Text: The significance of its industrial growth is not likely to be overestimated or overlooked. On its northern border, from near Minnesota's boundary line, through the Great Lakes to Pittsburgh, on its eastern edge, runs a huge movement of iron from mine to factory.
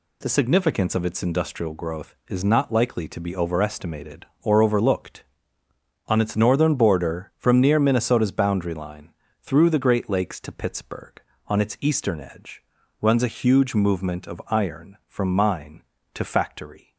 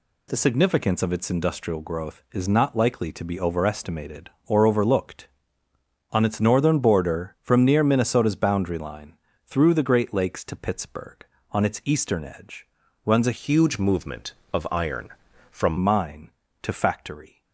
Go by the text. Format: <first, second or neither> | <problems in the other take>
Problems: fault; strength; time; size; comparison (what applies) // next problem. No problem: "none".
first | changes voice from "huge" to "from"; from 13.3 to 15.7 s; 2.4 s long